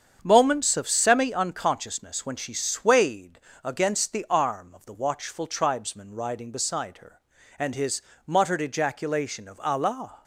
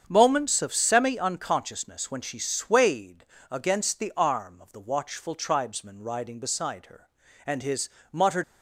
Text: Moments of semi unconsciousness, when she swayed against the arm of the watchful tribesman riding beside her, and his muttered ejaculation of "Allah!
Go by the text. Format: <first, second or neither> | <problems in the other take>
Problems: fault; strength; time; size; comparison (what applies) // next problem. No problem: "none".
first | starts louder than the rest; strong; until 1.0 s; 7.5 dB; strong in the first // pauses between "swayed" and "against"; slight; at 3.2 s; 0.24 s long; slight in the first // pauses between "his" and "muttered"; slight; at 7.8 s; 0.24 s long; slight in the first // stops before "ejaculation of Allah"; at 8.4 s